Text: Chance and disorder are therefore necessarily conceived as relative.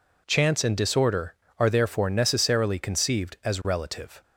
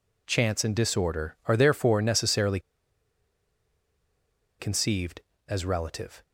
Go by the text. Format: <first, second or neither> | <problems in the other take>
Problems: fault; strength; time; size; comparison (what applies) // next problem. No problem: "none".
first | pauses between "necessarily" and "conceived"; strong; at 2.5 s; 2.0 s long